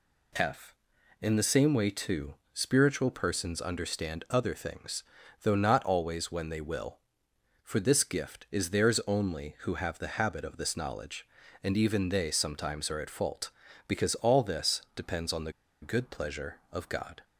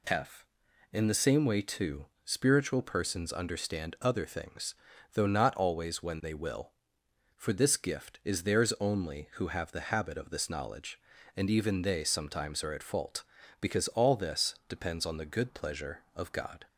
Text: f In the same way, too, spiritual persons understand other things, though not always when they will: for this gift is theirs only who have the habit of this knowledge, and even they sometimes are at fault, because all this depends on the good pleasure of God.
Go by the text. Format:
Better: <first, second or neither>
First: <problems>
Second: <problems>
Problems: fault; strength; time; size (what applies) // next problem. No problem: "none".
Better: second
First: pauses between "the" and "good"; slight; at 15.5 s; 0.30 s long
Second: none